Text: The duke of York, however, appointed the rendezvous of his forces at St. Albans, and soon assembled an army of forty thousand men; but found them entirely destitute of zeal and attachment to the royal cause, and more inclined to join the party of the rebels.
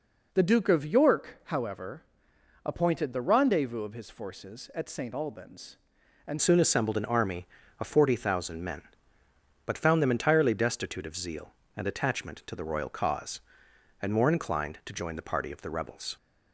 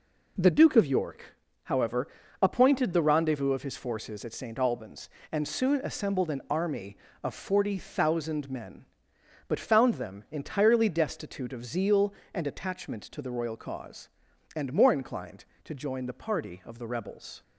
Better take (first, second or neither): second